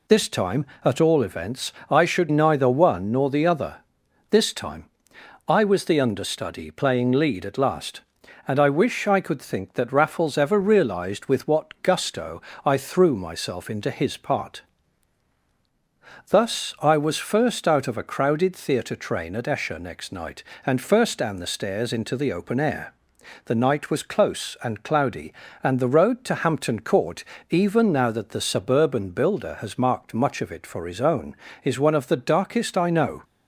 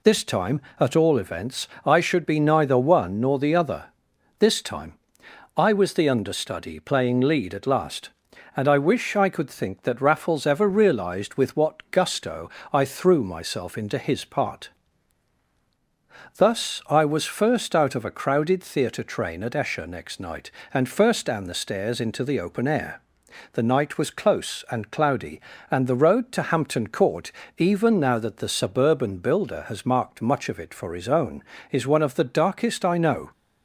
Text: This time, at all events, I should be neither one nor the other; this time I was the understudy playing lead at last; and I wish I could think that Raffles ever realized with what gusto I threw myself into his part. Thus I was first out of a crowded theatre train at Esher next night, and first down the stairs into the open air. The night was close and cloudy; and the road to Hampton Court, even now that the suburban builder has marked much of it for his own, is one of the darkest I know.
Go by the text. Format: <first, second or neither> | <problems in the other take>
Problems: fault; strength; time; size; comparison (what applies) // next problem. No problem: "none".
second | skips "be"; at 2.3 s // pauses between "time" and "I"; noticeable; at 4.8 s; 0.64 s long; noticeable in the second // pauses between "gusto" and "I"; slight; at 12.3 s; 0.24 s long; slight in the second